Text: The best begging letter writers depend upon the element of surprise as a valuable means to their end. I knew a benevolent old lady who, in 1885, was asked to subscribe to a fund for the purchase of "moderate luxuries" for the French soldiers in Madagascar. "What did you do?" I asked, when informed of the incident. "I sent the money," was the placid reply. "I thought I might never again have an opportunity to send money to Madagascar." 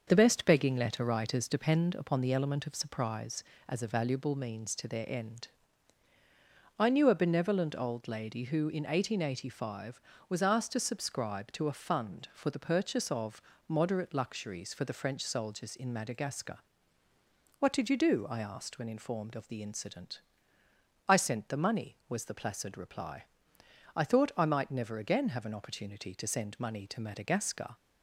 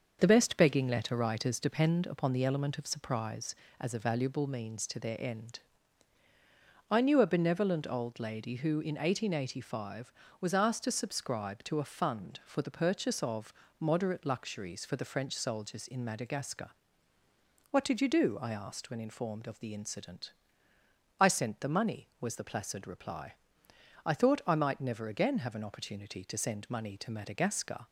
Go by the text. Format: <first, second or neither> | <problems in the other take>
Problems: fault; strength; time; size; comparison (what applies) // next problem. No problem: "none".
neither | starts louder than the rest; the same in both // pauses between "of" and "moderate"; slight; the same in both